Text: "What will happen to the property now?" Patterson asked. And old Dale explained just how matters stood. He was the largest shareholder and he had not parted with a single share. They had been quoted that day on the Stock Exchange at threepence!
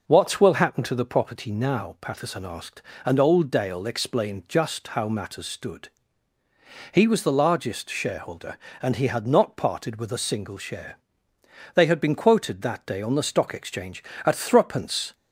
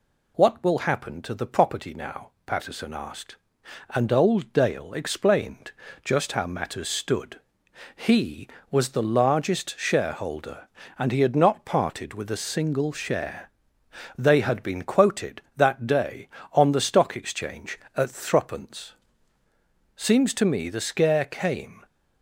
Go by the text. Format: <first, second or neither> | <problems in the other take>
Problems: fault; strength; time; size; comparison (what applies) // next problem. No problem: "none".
first | pauses between "explained" and "just"; slight; at 5.7 s; 0.32 s long // goes on to say "Seems to me the scare came"; strong; from 19.9 s on; 1.8 s long